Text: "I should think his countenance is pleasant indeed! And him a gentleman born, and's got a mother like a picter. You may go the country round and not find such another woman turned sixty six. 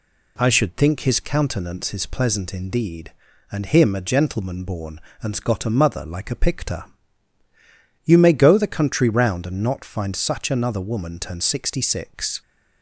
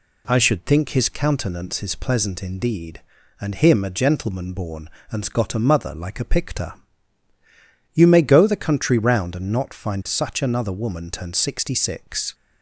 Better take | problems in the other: neither | none

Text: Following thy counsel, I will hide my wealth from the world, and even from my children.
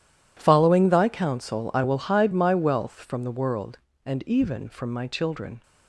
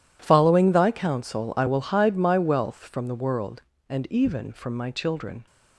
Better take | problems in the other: neither | none

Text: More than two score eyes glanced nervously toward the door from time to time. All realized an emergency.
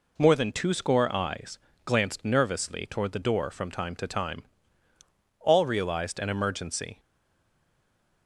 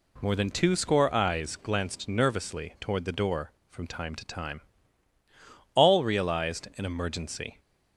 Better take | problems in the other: second | pauses between "eyes" and "glanced"; slight; at 1.5 s; 0.26 s long // stays silent after the last word; noticeable; from 6.9 s on; 1.3 s long

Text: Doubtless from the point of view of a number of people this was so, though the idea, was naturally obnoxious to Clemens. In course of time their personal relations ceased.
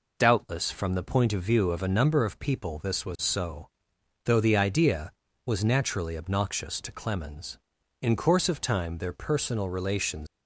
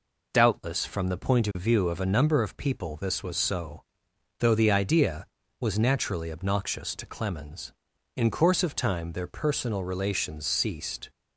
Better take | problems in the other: second | stops before "ceased"; at 10.2 s

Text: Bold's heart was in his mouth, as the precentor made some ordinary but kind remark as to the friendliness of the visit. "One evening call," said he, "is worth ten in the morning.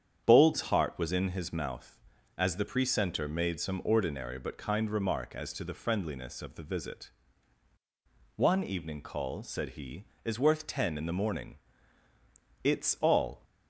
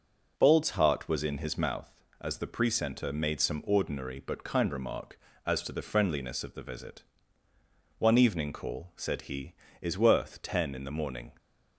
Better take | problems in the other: second | starts louder than the rest; strong; until 1.2 s; 8.5 dB // goes on to say "It's all"; noticeable; from 12.6 s on; 0.80 s long

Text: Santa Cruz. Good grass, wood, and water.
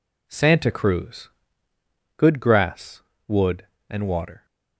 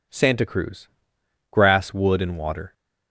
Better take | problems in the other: first | skips "Good"; at 1.1 s

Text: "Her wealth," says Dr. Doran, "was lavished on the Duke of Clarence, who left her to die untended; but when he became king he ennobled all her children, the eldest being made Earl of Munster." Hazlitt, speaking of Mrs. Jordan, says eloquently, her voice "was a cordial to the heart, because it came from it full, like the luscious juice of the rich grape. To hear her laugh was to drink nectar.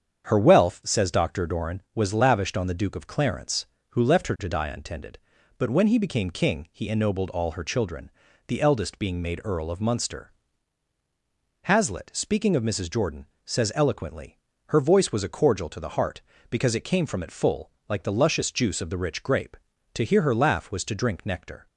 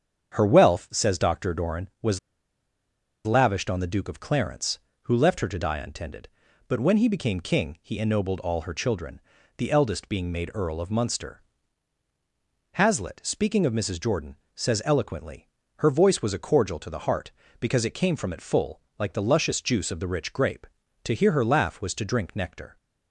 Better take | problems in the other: first | starts louder than the rest; strong; until 1.3 s; 8 dB; strong in the first // pauses between "was" and "lavished"; at 2.1 s; 1.0 s long

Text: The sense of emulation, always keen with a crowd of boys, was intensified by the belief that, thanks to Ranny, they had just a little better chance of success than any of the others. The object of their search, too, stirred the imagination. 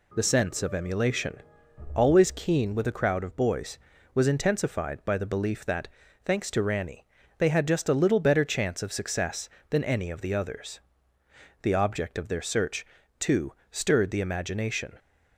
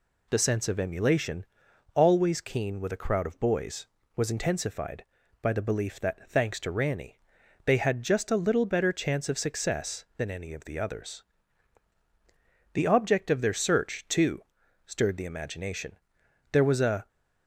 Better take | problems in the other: first | goes on to say "There was a"; from 16.5 s on; 0.56 s long

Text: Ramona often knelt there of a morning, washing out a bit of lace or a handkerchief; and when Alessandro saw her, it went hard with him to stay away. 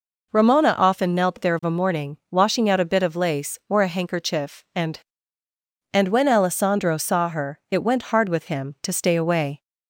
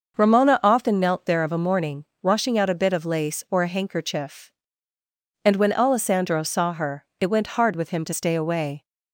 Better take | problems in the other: second | says "and" twice; at 5.9 s

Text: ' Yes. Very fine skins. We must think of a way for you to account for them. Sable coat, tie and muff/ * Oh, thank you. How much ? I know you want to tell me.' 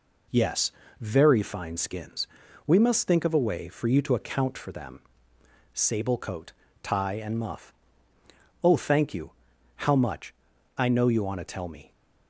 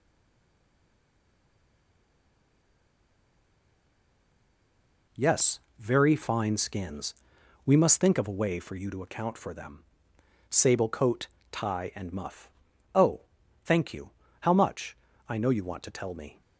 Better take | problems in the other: first | stays silent before the first word; strong; until 5.0 s; 5.0 s long

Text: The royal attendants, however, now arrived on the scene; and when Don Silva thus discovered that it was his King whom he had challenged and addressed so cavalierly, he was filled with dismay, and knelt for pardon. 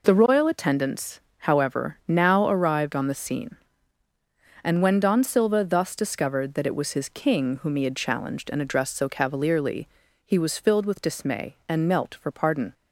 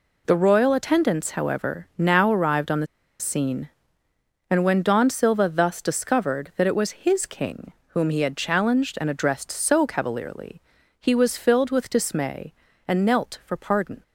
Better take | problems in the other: first | pauses between "the" and "scene"; slight; at 2.8 s; 0.35 s long // pauses between "King" and "whom"; slight; at 7.7 s; 0.20 s long

